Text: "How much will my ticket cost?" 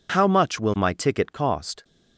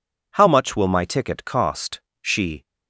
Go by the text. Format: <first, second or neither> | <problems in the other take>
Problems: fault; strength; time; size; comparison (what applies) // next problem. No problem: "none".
first | goes on to say "she"; slight; from 2.2 s on; 0.44 s long